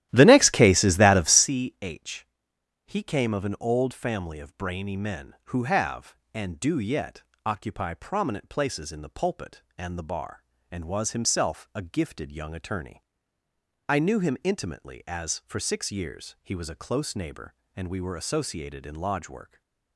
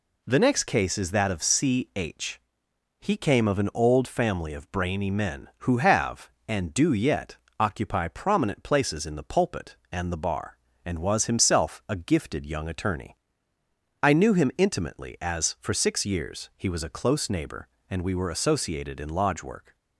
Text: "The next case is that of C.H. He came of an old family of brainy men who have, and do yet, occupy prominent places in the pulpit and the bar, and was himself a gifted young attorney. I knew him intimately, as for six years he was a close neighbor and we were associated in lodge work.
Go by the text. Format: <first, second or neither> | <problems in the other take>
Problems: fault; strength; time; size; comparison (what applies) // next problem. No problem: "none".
second | starts louder than the rest; strong; until 1.5 s; 13.5 dB // stays silent after the last word; slight; from 19.4 s on; 0.5 s long